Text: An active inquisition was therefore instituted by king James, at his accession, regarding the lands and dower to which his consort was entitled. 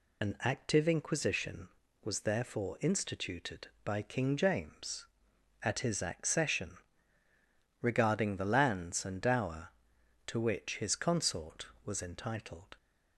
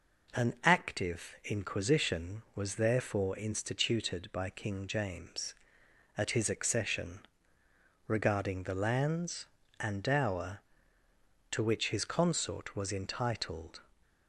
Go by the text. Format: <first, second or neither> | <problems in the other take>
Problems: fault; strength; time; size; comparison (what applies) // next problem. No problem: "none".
second | loses the start of "An"; at 0.2 s; 45 ms